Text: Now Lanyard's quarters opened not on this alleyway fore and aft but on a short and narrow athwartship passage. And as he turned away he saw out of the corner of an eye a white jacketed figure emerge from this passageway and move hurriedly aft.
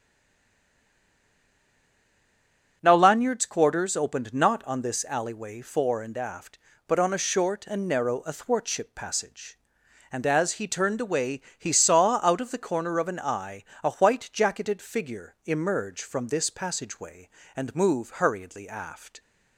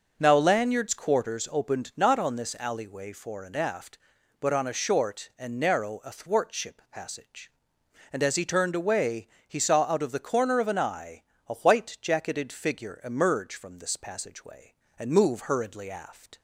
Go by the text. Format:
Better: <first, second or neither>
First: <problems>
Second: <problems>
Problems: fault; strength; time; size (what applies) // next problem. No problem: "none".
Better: second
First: stays silent before the first word; strong; until 2.8 s; 2.8 s long // starts louder than the rest; strong; until 3.8 s; 7.5 dB // pauses between "away" and "he"; slight; at 11.4 s; 0.18 s long // pauses between "eye" and "a"; slight; at 13.6 s; 0.20 s long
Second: pauses between "away" and "he"; slight; at 9.2 s; 0.20 s long // pauses between "eye" and "a"; slight; at 11.2 s; 0.26 s long